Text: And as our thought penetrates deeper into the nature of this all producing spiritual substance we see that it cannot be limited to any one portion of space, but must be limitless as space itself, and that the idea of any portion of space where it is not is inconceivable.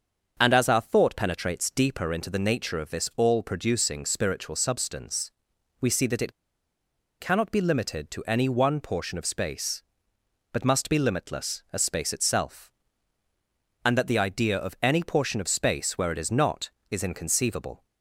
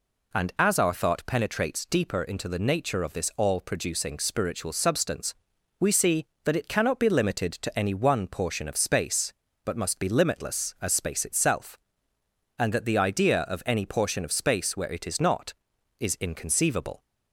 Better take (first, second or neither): second